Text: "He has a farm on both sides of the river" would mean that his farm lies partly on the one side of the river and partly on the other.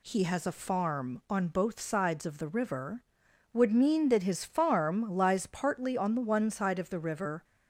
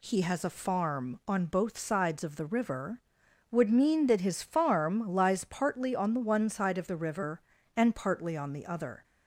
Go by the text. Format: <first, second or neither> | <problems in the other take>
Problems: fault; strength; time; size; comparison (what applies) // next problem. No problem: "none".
second | stops before "and partly on the other"; at 7.4 s